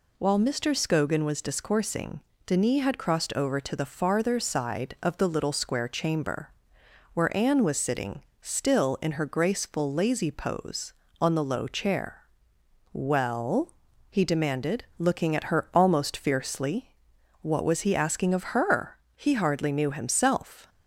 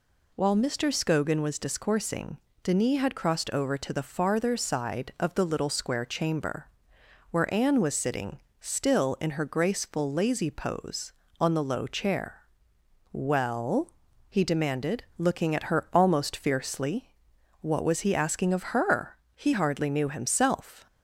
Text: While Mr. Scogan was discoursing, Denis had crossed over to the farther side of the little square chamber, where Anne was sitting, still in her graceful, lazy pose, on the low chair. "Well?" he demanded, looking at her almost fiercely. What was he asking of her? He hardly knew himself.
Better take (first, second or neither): neither